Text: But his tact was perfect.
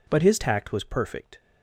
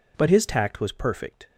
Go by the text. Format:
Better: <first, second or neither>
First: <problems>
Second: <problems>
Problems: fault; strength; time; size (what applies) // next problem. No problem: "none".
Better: neither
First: none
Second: none